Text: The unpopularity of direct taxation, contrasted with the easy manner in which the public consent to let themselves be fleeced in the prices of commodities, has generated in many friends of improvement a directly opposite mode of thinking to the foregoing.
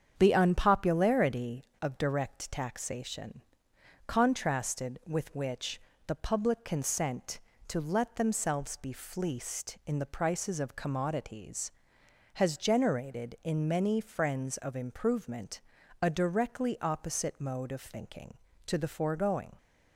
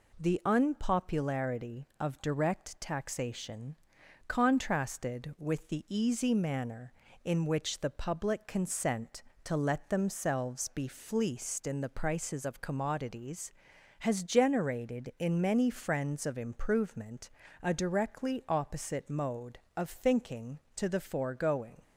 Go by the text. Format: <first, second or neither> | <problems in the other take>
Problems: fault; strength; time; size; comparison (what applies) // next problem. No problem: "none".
second | starts louder than the rest; strong; until 1.1 s; 7.5 dB // skips "the easy manner in"; at 5.3 s // pauses between "which" and "the"; slight; at 5.7 s; 0.28 s long // pauses between "improvement" and "a"; at 15.6 s; 0.40 s long; slight in the second